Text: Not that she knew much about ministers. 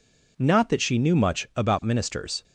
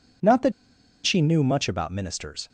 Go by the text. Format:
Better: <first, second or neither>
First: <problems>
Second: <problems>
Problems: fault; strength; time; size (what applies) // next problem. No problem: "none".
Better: first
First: none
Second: pauses between "that" and "she"; noticeable; at 0.5 s; 0.53 s long